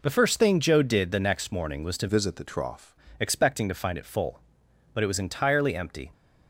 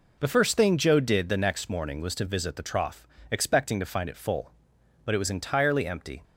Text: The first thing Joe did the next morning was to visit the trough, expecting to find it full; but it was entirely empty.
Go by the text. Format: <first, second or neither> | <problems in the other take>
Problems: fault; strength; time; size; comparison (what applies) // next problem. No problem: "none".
second | changes voice from "visit" to "trough"; from 2.0 to 2.9 s; 0.9 s long